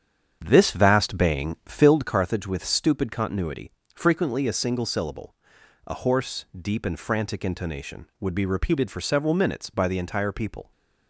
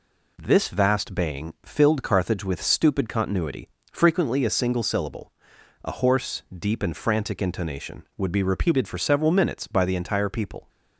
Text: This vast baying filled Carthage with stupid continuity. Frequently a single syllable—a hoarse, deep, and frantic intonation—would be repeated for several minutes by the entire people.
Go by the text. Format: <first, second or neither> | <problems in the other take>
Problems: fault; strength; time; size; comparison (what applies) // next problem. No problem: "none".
second | starts louder than the rest; strong; until 2.1 s; 8 dB